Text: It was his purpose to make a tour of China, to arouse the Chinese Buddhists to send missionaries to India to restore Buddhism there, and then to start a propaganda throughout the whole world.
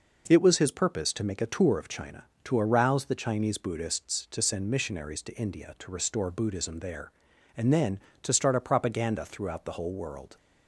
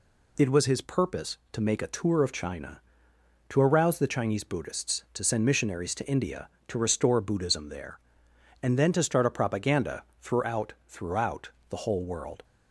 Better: first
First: none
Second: pauses between "propaganda" and "throughout"; slight; at 10.0 s; 0.16 s long // says "throughout" twice; at 10.8 s

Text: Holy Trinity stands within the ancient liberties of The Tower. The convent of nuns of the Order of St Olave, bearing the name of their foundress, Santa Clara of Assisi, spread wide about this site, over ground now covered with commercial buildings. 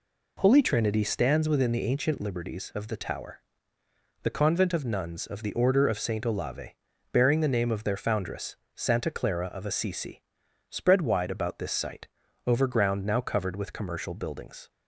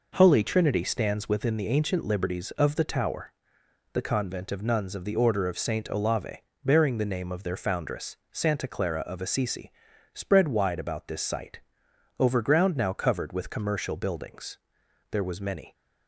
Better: first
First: none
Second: goes on to say "There was many"; noticeable; from 15.0 s on; 0.64 s long

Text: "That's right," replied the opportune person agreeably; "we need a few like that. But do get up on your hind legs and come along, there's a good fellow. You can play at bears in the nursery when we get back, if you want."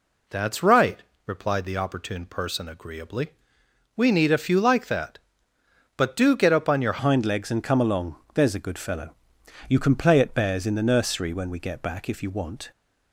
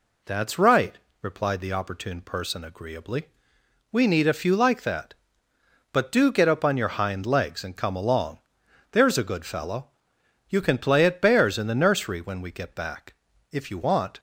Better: second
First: changes voice at "hind"; from 6.9 s on; 5.8 s long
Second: none

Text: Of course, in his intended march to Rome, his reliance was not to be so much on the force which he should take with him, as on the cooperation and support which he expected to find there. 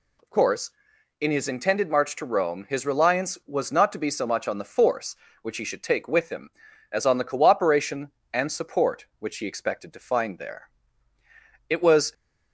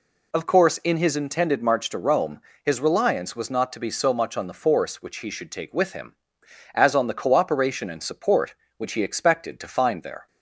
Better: second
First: goes on to say "It was"; slight; from 11.6 s on; 0.44 s long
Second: none

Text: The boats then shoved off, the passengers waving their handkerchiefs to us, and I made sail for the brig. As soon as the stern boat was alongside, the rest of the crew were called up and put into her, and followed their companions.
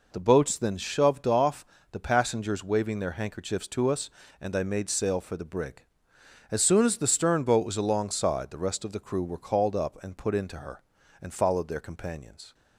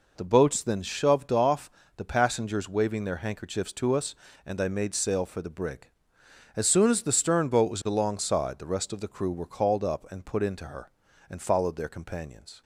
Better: neither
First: none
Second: none

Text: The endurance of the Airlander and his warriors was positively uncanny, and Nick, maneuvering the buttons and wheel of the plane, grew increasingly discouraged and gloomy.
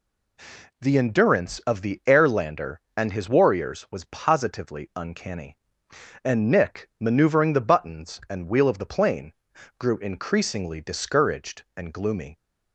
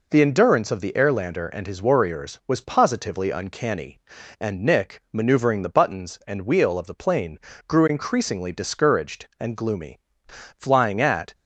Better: first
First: none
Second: goes on to say "Flying at"; noticeable; from 10.5 s on; 0.76 s long

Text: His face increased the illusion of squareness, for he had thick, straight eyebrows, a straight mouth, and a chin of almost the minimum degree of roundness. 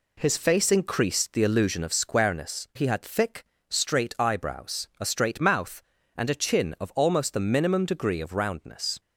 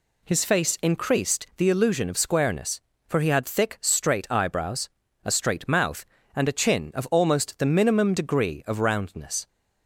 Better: second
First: skips "for"; at 2.7 s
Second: none

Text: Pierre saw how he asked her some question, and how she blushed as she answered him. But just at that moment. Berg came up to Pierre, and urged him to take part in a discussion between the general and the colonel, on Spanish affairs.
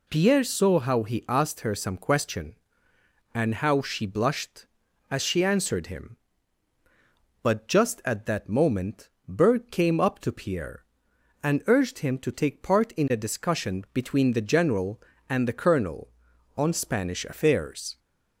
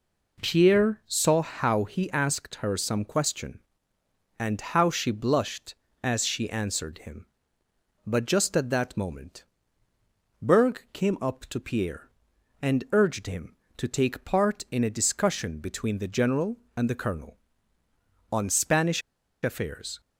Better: first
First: none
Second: pauses between "Spanish" and "affairs"; at 19.0 s; 0.42 s long

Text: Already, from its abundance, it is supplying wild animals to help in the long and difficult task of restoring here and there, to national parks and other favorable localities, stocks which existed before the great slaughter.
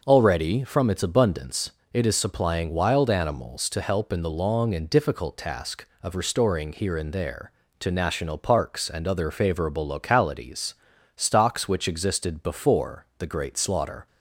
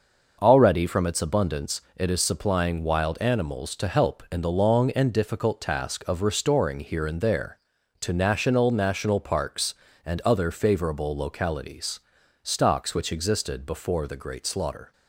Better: first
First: none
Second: says "national" twice; at 8.7 s

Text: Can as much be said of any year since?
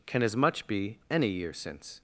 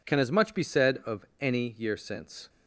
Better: second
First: skips "said of"; at 1.0 s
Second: none

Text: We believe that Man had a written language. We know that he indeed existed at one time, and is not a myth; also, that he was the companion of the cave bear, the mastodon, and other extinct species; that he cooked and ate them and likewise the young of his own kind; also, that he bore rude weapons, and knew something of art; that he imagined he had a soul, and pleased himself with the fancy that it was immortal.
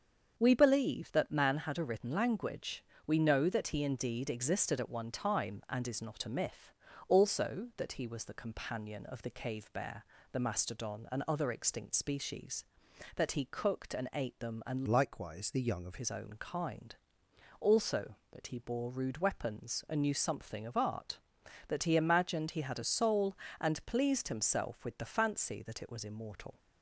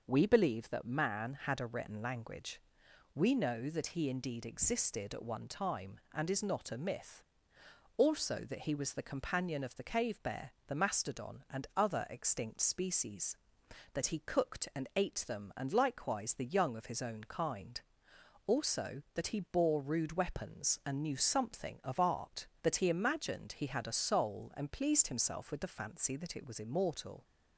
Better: second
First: starts louder than the rest; until 1.3 s; 7 dB // changes voice from "likewise" to "of"; from 14.8 to 15.9 s; 1.1 s long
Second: none

